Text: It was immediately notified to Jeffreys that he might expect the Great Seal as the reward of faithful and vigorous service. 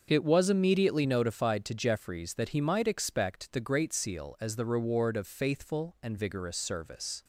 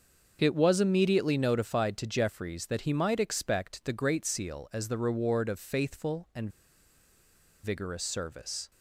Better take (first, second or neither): first